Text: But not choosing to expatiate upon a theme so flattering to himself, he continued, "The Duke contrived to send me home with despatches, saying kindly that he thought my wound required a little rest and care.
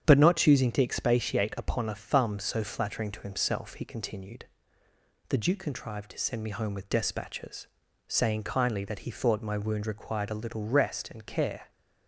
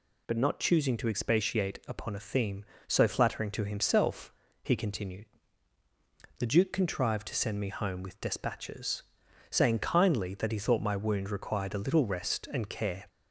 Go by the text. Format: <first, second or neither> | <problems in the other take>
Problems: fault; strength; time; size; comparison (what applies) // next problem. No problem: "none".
second | starts louder than the rest; strong; until 1.0 s; 8.5 dB // says "thumb" for "theme"; at 1.9 s